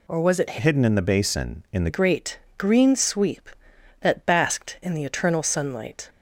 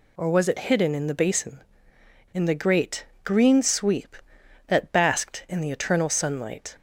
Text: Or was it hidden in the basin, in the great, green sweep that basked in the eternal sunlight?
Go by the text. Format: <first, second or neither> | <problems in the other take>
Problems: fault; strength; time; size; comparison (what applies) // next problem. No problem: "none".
second | changes voice from "hidden" to "the"; from 0.5 to 1.8 s; 1.3 s long